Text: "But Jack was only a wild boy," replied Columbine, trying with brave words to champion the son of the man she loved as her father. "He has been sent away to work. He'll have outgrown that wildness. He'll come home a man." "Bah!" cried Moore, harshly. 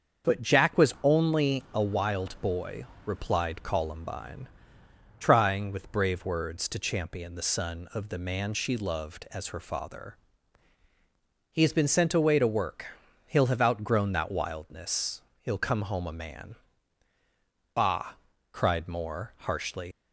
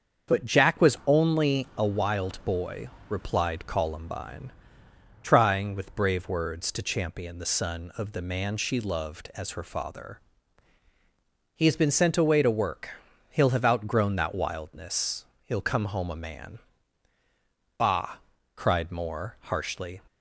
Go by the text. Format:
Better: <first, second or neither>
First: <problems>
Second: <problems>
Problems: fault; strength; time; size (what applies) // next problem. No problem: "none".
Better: second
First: starts louder than the rest; until 1.3 s; 7 dB // leaves "harshly" unfinished; at 19.9 s; 115 ms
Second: starts louder than the rest; until 1.4 s; 7 dB